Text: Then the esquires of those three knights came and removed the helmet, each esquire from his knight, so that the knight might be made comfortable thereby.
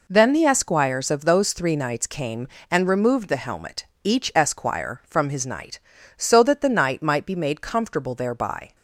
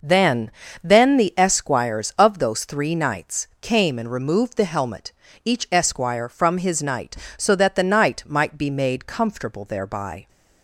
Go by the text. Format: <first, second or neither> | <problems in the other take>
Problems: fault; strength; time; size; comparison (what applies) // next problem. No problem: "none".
first | says "Then" twice; at 0.8 s